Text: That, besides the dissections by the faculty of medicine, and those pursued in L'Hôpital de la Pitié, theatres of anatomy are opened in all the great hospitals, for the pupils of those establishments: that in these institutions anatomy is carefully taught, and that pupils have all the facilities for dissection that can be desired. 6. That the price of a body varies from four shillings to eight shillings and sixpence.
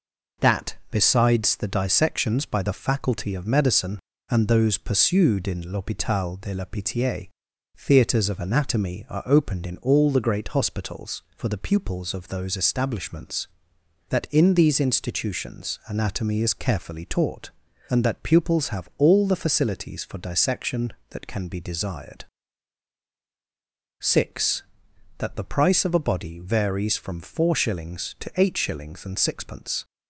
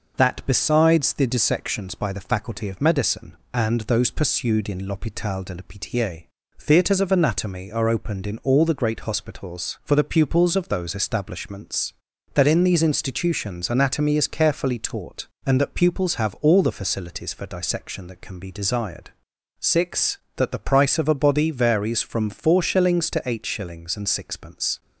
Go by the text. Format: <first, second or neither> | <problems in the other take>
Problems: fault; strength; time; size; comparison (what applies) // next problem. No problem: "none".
neither | none